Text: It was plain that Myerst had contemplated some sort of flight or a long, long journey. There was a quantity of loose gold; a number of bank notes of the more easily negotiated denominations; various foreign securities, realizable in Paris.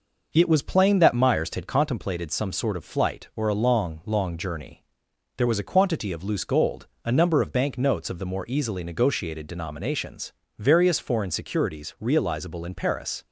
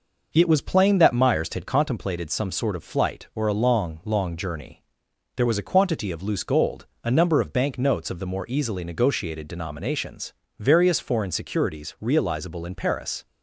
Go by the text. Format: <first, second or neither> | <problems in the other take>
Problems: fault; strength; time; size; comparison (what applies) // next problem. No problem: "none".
neither | none